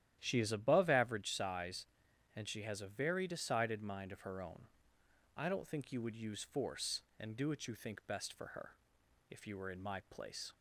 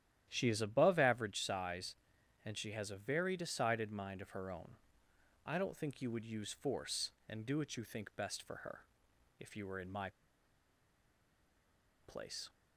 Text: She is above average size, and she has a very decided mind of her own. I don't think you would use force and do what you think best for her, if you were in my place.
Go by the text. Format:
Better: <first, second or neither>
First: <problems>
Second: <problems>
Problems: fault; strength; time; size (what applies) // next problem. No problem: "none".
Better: first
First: starts louder than the rest; strong; until 1.2 s; 11.5 dB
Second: starts louder than the rest; strong; until 1.2 s; 11.5 dB // pauses between "my" and "place"; strong; at 10.1 s; 1.9 s long